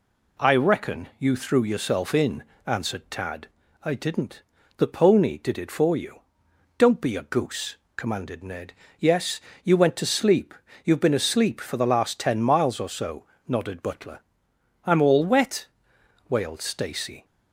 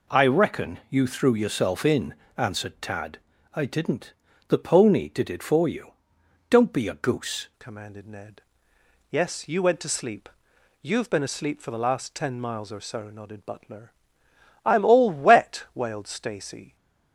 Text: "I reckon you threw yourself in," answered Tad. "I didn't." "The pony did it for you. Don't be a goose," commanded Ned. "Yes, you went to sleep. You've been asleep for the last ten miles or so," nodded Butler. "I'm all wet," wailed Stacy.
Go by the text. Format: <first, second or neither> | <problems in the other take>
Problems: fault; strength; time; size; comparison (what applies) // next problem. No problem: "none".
first | changes voice at "commanded"; from 7.5 s on; 9.2 s long